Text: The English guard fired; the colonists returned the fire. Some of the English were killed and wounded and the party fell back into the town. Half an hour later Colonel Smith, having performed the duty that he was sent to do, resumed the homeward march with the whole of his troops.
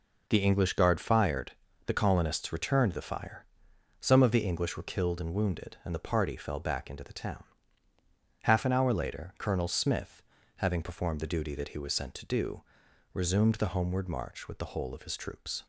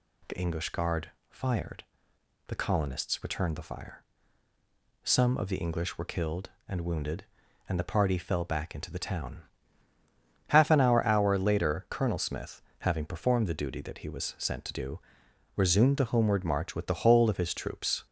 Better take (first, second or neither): first